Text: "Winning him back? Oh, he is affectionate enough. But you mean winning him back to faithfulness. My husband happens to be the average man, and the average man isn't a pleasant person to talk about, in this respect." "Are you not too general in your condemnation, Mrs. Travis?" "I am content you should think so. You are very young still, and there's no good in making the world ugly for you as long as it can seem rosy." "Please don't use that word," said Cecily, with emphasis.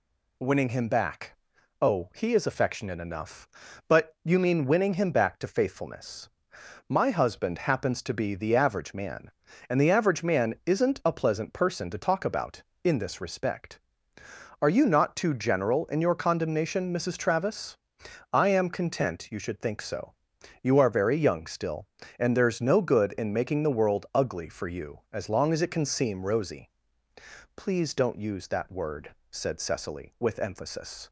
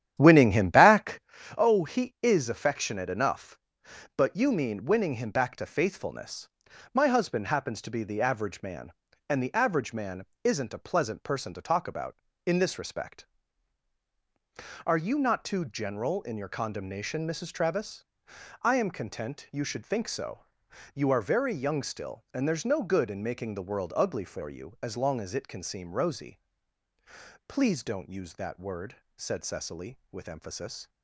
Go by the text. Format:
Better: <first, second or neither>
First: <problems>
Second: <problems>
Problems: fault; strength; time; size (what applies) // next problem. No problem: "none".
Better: first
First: none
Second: starts louder than the rest; strong; until 1.3 s; 11 dB // pauses between "man" and "isn't"; slight; at 10.2 s; 0.18 s long